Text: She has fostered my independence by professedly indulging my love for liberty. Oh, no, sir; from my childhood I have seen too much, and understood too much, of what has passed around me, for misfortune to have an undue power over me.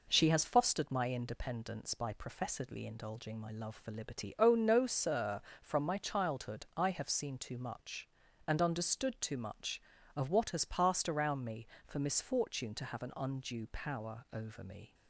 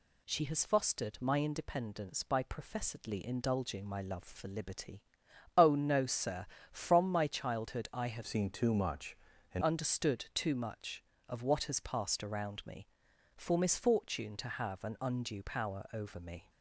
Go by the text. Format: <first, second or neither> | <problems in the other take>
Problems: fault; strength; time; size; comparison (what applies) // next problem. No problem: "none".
first | changes voice from "seen" to "and"; from 8.2 to 9.6 s; 1.4 s long